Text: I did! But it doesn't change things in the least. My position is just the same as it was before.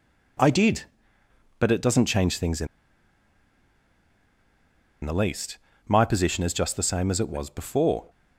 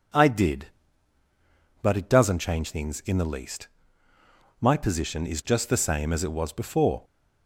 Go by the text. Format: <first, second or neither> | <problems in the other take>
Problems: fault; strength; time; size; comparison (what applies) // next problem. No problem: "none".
second | pauses between "in" and "the"; strong; at 2.6 s; 2.3 s long